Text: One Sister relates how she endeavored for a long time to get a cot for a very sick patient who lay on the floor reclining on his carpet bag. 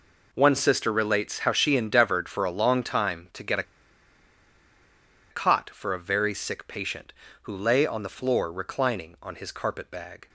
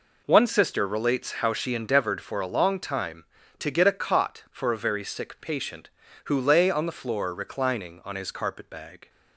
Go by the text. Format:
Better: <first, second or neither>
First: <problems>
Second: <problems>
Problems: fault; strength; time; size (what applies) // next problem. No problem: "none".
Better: second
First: pauses between "a" and "cot"; strong; at 3.6 s; 1.6 s long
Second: none